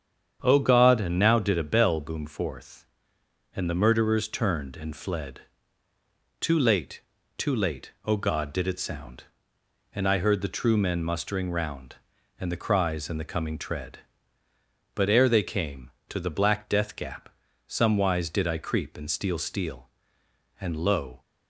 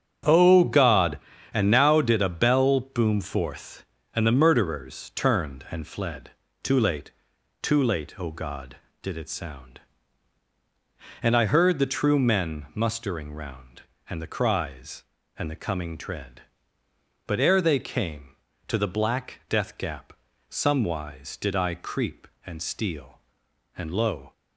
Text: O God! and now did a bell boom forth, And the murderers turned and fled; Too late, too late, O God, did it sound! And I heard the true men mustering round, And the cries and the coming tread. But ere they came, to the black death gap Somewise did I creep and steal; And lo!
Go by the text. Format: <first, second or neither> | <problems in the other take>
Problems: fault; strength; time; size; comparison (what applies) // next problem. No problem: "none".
second | starts louder than the rest; strong; until 1.4 s; 8 dB; strong in the second // pauses between "gap" and "Somewise"; at 17.2 s; 0.38 s long; slight in the second // says "steal" twice; at 19.3 s